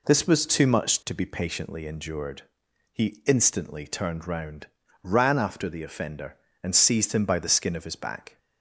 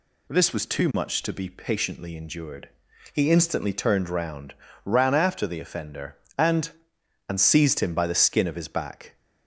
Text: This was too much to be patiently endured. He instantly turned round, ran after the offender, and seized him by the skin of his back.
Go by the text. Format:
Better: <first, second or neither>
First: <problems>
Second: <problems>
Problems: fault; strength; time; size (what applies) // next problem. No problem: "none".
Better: first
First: none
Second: says "and" twice; at 7.2 s